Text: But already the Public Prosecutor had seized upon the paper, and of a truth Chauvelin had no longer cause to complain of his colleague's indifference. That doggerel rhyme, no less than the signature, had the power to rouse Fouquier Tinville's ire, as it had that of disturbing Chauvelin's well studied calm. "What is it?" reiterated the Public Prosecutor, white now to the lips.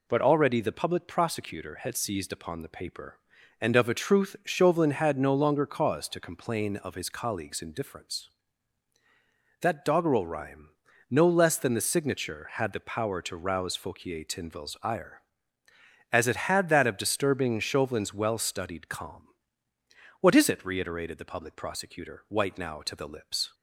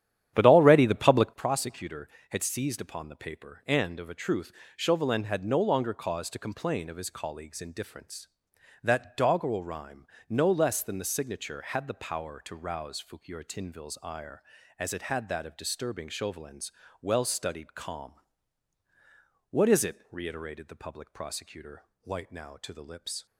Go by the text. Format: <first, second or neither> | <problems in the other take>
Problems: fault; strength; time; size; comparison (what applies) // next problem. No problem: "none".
first | starts louder than the rest; strong; until 1.4 s; 10.5 dB // pauses between "truth" and "Chauvelin"; slight; at 4.5 s; 0.24 s long // pauses between "Chauvelin's" and "well"; slight; at 16.7 s; 0.30 s long